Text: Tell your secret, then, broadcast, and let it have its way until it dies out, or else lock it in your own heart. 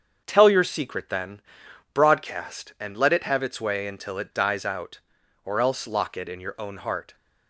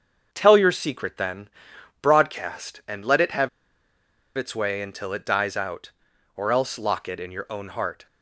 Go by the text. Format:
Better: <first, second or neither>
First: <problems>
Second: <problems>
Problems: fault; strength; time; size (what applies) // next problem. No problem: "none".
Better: first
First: starts louder than the rest; until 1.2 s; 7 dB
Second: starts louder than the rest; until 1.3 s; 7 dB // pauses between "have" and "its"; noticeable; at 3.4 s; 0.89 s long